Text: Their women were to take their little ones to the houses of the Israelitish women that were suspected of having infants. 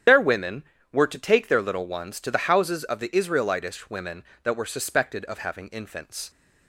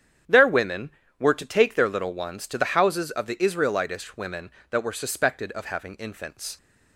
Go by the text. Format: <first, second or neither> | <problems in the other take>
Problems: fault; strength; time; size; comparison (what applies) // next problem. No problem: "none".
second | loses the start of "Their"; at 0.0 s; 75 ms // starts louder than the rest; strong; until 1.3 s; 9.5 dB; strong in the second